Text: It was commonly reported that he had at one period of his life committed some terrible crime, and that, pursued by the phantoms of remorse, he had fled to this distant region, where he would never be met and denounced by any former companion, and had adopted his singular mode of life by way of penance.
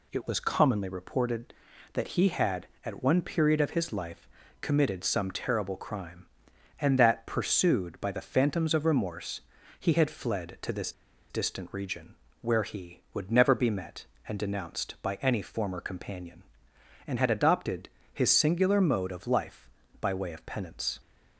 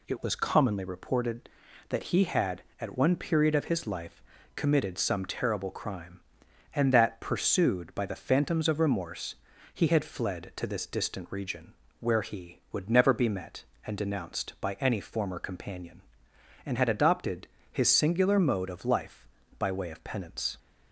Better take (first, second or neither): second